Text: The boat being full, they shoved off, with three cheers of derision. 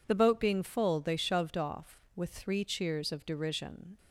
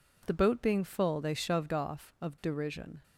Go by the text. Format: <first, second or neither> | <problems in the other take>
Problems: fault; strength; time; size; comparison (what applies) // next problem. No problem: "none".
first | skips "with three cheers"; at 2.1 s